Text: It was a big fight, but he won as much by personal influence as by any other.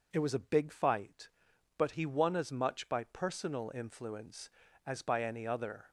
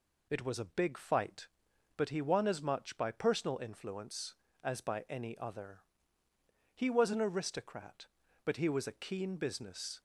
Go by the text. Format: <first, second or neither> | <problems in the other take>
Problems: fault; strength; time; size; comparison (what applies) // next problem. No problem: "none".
first | goes on to say "He was an aristocrat but he was a keen business"; strong; from 6.7 s on; 3.2 s long